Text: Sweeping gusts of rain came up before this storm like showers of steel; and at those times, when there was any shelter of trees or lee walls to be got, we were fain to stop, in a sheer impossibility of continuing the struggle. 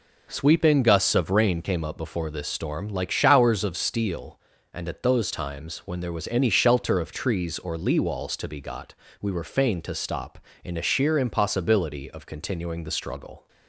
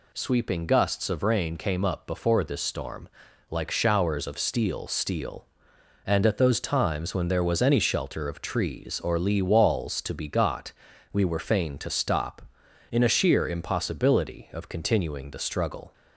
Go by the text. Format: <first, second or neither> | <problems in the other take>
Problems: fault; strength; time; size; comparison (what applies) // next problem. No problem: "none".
first | pauses between "storm" and "like"; at 3.0 s; 0.40 s long // says "steel" twice; at 4.8 s